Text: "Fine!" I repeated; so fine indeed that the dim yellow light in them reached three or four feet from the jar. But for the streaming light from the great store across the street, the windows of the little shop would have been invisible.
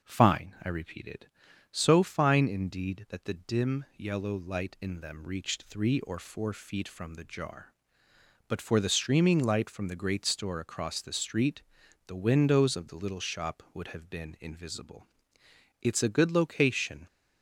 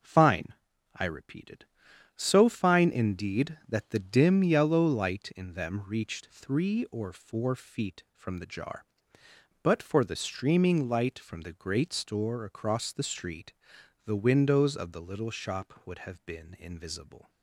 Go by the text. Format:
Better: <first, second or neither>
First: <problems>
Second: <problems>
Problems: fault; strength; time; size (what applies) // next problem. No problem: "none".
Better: second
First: starts louder than the rest; until 1.0 s; 6 dB // goes on to say "It's a good location"; noticeable; from 15.8 s on; 1.2 s long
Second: none